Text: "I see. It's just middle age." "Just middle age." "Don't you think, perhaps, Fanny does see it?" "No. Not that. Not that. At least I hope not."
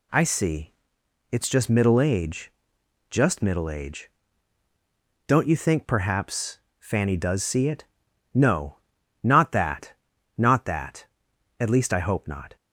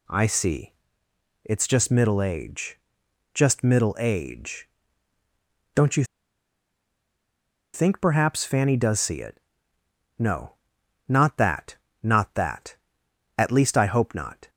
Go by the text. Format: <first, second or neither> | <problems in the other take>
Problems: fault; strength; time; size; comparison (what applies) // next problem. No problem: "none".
first | pauses between "you" and "think"; strong; at 6.0 s; 1.7 s long